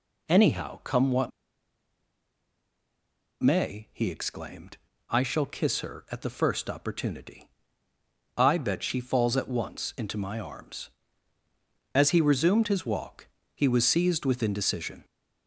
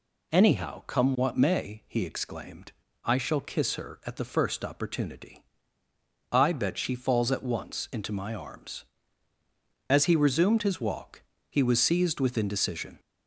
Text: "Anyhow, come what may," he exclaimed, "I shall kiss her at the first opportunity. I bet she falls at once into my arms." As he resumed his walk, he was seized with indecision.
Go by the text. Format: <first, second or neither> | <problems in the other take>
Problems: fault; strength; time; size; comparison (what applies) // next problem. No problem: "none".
second | pauses between "what" and "may"; strong; at 1.3 s; 2.1 s long